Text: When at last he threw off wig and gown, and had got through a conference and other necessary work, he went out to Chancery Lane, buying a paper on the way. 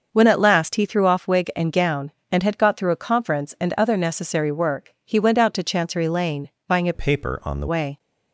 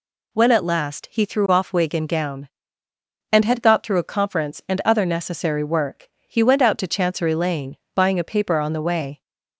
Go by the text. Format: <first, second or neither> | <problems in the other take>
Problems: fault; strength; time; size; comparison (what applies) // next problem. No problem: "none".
second | starts louder than the rest; until 1.1 s; 6.5 dB // changes voice from "paper" to "the"; from 6.9 to 7.6 s; 0.7 s long